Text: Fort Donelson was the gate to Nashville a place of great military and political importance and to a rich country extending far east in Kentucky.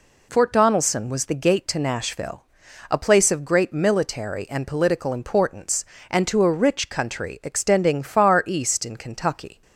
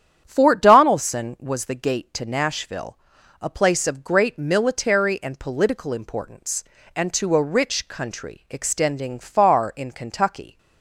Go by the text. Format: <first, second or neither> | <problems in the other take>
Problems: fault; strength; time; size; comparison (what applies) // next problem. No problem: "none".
first | starts louder than the rest; strong; until 1.2 s; 9.5 dB // pauses between "Nashville" and "a"; at 2.9 s; 0.44 s long; noticeable in the first // skips "east"; at 9.7 s